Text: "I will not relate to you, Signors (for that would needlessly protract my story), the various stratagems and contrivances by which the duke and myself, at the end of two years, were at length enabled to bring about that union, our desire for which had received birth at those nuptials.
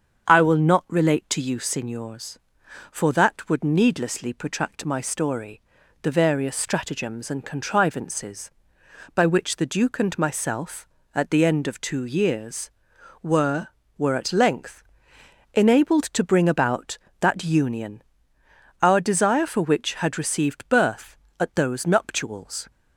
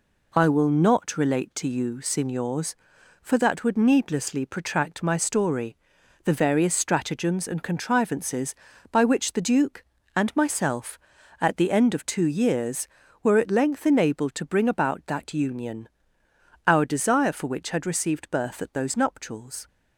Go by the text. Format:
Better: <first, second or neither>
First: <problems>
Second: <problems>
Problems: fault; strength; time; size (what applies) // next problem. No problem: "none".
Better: second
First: starts louder than the rest; strong; until 1.3 s; 7.5 dB // says "were" twice; at 13.9 s // pauses between "length" and "enabled"; noticeable; at 14.8 s; 0.70 s long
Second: none